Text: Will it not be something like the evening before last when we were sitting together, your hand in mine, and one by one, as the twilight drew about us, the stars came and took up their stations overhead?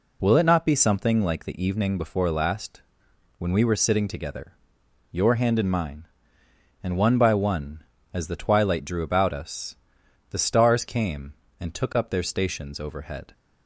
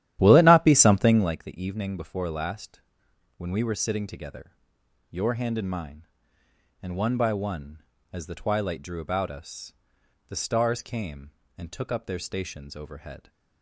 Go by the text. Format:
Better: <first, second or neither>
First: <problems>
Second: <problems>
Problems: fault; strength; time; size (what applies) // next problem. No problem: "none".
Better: first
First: pauses between "last" and "when"; noticeable; at 2.8 s; 0.56 s long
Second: starts louder than the rest; strong; until 1.4 s; 12 dB // pauses between "last" and "when"; noticeable; at 2.8 s; 0.56 s long